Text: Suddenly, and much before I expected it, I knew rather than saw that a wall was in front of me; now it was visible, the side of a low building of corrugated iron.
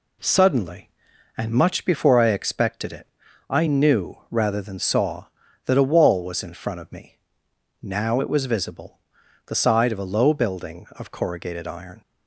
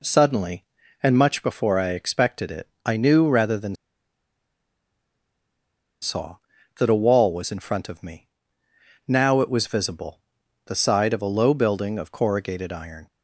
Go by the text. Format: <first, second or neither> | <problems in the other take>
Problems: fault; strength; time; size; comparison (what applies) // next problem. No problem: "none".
first | pauses between "than" and "saw"; strong; at 3.7 s; 2.2 s long